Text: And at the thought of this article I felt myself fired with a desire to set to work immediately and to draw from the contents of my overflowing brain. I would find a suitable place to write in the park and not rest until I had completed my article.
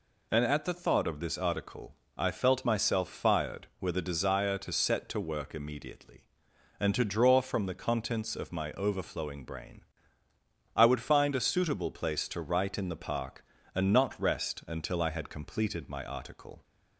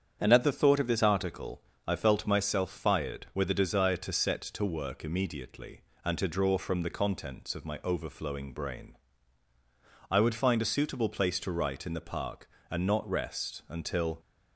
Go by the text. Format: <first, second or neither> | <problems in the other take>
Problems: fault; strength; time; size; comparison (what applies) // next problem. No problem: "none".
first | starts louder than the rest; strong; until 1.2 s; 8 dB // pauses between "article" and "I"; slight; at 1.6 s; 0.26 s long; slight in the first // stops before "I had completed my article"; at 14.1 s